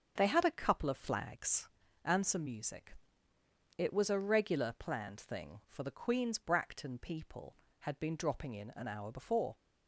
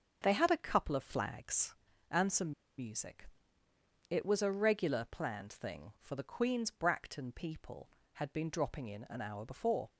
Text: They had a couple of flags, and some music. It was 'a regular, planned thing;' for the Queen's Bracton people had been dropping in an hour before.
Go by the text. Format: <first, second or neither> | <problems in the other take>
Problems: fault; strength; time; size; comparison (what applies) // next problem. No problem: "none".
first | starts louder than the rest; until 1.2 s; 6.5 dB; also in the first // pauses between "some" and "music"; slight; at 2.5 s; 0.25 s long